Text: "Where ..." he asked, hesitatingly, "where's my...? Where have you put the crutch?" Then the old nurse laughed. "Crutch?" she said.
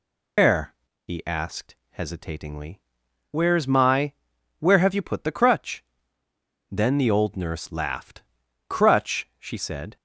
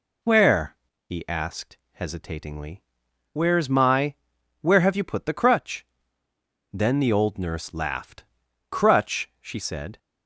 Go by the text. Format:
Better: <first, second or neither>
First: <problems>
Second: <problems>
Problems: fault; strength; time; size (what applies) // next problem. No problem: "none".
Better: second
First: loses the start of "Where"; at 0.3 s; 155 ms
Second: none